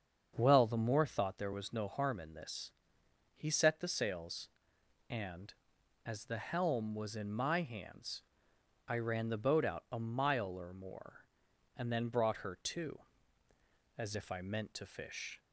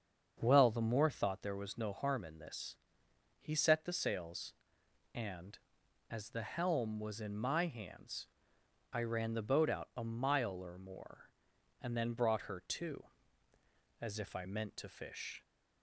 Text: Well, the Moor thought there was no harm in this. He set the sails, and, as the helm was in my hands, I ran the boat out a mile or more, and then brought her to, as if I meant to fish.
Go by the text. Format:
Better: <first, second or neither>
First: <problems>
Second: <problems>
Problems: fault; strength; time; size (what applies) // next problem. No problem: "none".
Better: neither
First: starts louder than the rest; until 1.3 s; 7 dB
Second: starts louder than the rest; until 1.4 s; 7 dB